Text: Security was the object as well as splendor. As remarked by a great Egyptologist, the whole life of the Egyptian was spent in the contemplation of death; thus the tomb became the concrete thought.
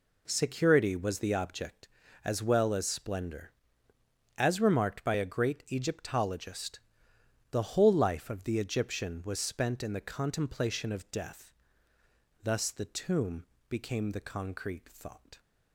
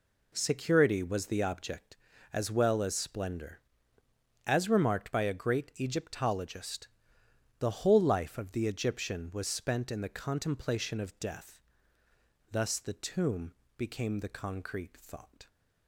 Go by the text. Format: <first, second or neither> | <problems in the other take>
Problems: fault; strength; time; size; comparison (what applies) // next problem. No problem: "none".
neither | pauses between "tomb" and "became"; slight; the same in both